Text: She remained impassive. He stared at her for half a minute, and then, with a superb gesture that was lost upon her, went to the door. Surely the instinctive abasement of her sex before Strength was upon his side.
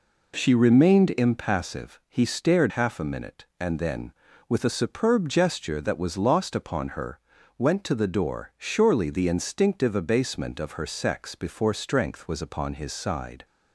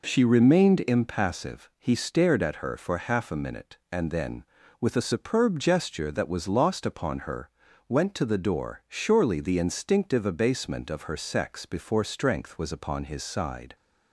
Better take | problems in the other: second | skips "at her for"; at 2.7 s

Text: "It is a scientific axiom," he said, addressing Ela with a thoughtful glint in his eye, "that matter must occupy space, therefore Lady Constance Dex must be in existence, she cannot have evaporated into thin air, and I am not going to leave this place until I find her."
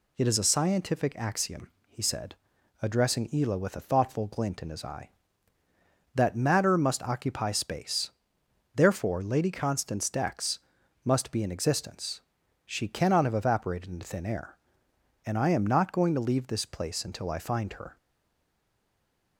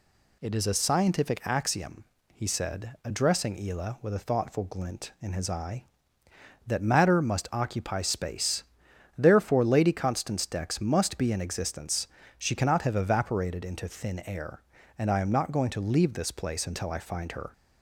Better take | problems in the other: second | pauses between "Dex" and "must"; at 10.5 s; 0.44 s long // stays silent after the last word; noticeable; from 17.9 s on; 1.4 s long

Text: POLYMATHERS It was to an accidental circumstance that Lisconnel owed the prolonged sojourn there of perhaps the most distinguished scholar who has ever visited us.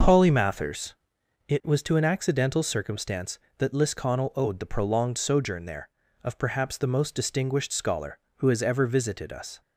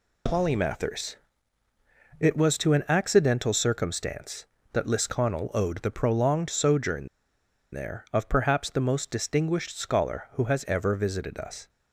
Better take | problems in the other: first | pauses between "POLYMATHERS" and "It"; at 1.1 s; 1.0 s long; noticeable in the first // pauses between "sojourn" and "there"; noticeable; at 7.0 s; 0.65 s long

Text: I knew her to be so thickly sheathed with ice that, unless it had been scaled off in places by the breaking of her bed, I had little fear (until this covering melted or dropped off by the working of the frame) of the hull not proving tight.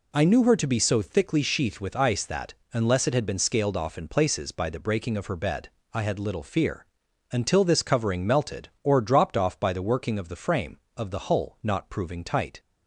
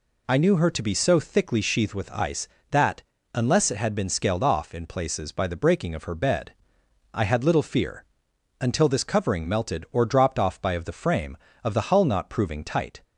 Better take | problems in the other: first | skips "the working"; at 10.7 s

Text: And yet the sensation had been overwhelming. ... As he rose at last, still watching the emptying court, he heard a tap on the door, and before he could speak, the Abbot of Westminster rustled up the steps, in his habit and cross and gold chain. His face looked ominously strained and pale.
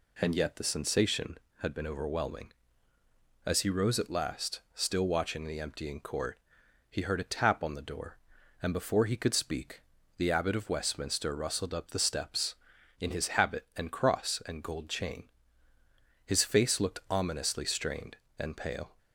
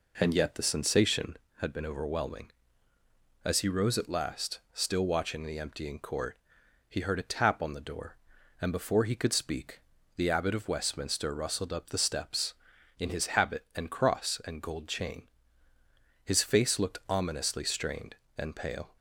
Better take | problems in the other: first | starts louder than the rest; noticeable; until 1.5 s; 4 dB

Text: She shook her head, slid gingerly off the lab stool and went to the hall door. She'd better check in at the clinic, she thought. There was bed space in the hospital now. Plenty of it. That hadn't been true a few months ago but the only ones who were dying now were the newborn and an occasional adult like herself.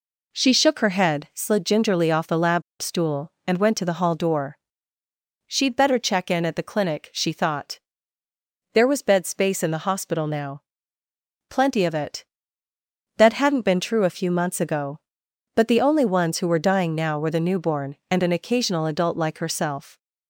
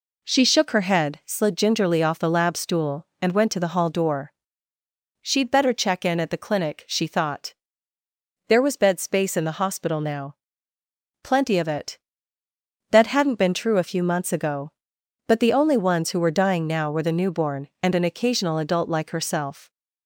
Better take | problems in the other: second | pauses between "lab" and "stool"; slight; at 2.6 s; 0.19 s long

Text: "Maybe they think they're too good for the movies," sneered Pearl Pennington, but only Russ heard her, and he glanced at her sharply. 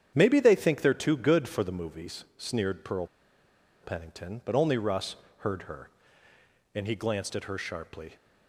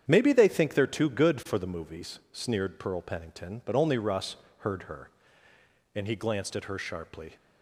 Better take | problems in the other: second | starts louder than the rest; strong; until 1.1 s; 8.5 dB; strong in the second // pauses between "Pearl" and "Pennington"; noticeable; at 3.0 s; 0.75 s long // pauses between "Russ" and "heard"; slight; at 5.1 s; 0.24 s long; slight in the second

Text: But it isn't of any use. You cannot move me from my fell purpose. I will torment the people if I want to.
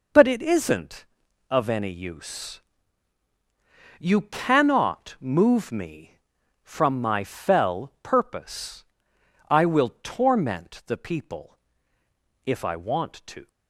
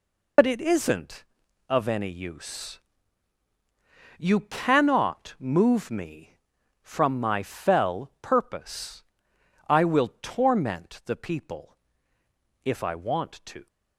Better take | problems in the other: first | loses the start of "But"; at 0.3 s; 60 ms // pauses between "people" and "if"; noticeable; at 11.7 s; 0.88 s long; noticeable in the first

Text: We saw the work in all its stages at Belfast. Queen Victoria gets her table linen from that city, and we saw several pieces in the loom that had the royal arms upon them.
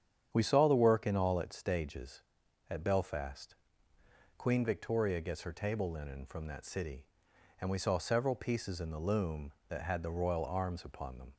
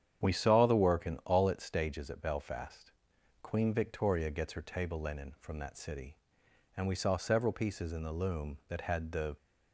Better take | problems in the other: first | starts louder than the rest; strong; until 1.3 s; 9 dB; strong in the first // stops before "royal arms upon them"; at 9.3 s

